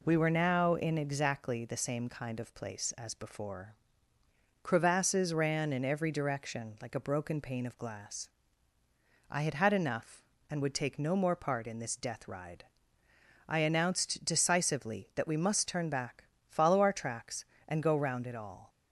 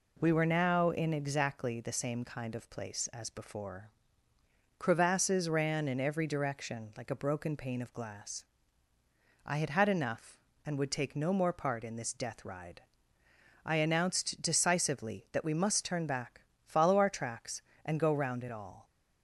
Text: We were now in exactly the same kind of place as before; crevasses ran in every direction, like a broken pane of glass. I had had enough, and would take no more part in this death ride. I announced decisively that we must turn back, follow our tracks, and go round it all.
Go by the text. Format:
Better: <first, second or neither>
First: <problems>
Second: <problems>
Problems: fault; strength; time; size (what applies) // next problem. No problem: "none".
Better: neither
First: none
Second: none